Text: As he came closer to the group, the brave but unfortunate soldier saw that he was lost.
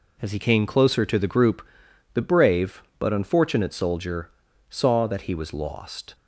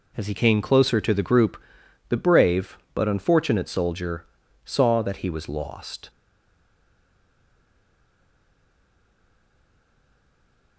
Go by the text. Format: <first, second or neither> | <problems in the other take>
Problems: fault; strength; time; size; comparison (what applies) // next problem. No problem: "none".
first | pauses between "soldier" and "saw"; at 4.2 s; 0.40 s long; also in the first // stays silent after the last word; strong; from 6.0 s on; 4.7 s long